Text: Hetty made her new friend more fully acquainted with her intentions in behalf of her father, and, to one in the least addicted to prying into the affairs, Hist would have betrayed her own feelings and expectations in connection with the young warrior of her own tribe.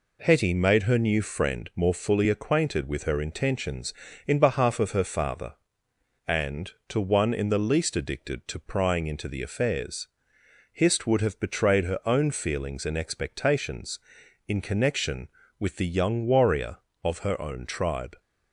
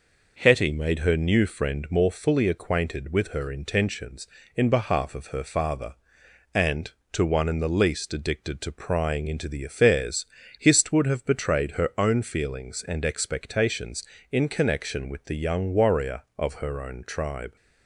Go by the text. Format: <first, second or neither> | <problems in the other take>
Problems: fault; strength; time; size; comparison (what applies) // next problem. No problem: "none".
neither | none